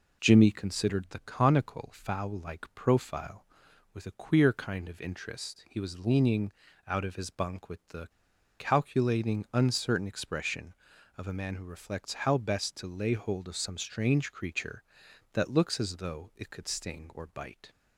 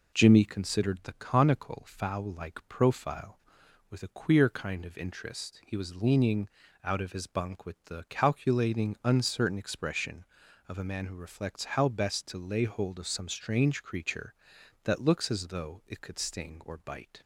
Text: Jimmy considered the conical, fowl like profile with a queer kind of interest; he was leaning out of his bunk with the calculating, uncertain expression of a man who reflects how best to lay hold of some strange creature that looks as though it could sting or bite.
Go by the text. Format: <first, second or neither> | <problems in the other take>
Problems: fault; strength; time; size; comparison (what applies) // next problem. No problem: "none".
second | pauses between "leaning" and "out"; slight; at 6.5 s; 0.34 s long; slight in the second // pauses between "the" and "calculating"; noticeable; at 8.0 s; 0.51 s long